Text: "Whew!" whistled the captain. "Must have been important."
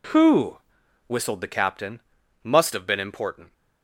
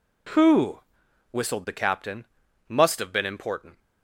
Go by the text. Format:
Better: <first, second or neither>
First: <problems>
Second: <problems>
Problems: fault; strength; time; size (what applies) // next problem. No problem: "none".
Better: neither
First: none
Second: none